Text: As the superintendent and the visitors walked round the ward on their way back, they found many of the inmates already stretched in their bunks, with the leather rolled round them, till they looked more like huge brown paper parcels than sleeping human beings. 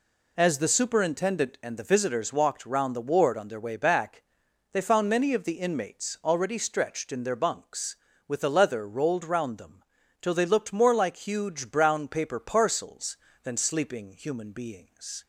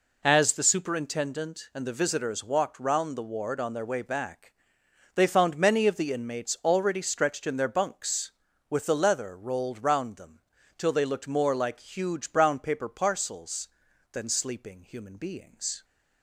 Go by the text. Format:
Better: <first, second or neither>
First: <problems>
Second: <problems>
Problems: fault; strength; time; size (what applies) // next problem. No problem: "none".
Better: neither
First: none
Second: none